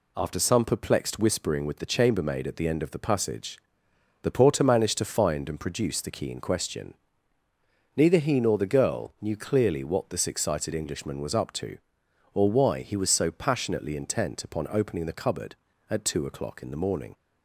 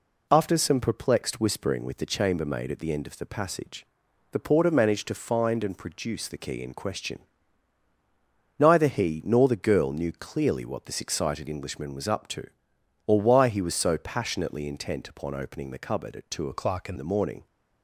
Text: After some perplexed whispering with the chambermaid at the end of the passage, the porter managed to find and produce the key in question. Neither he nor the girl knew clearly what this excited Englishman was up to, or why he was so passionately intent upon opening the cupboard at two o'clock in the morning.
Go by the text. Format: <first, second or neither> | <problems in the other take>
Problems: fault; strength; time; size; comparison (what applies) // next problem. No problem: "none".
first | changes voice from "o'clock" to "in"; from 16.5 to 16.9 s; 0.4 s long